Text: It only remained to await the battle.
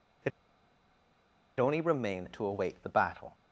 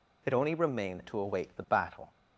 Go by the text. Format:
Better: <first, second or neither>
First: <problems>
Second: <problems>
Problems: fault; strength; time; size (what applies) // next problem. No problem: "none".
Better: second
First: pauses between "It" and "only"; strong; at 0.3 s; 1.2 s long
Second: none